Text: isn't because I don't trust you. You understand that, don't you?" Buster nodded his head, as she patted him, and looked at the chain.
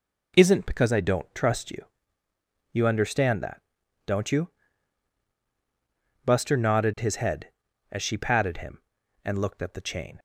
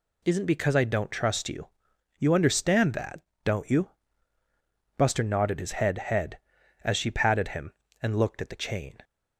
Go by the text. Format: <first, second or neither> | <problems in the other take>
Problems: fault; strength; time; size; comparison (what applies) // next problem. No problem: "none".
first | says "head" twice; at 5.9 s